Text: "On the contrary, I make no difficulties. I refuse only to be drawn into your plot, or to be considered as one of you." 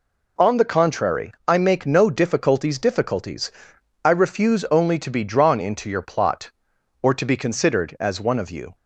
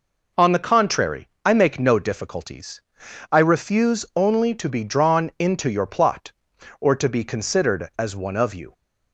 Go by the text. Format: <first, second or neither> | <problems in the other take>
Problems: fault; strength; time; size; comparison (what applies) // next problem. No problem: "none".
second | says "difficulties" twice; at 2.7 s